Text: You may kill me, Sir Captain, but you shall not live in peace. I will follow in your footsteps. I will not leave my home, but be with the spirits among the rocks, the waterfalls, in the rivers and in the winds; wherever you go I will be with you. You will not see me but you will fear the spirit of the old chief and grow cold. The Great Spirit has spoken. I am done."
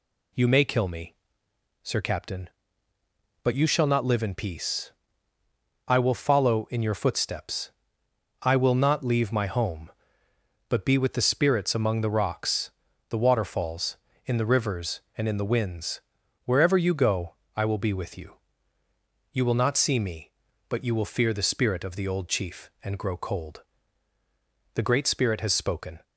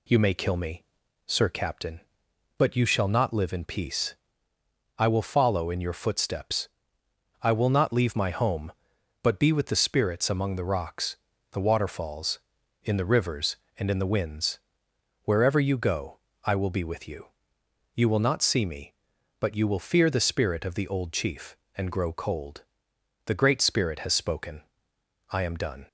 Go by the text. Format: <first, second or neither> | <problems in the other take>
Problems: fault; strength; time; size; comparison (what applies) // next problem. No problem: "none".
second | pauses between "go" and "I"; slight; at 17.3 s; 0.22 s long; slight in the second // stops before "I am done"; at 26.0 s